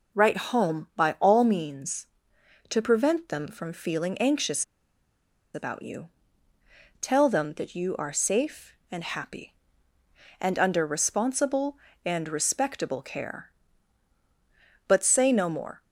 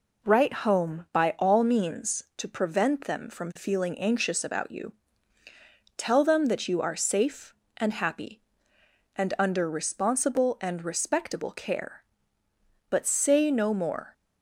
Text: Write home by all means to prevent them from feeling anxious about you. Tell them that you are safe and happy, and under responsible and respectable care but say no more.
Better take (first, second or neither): second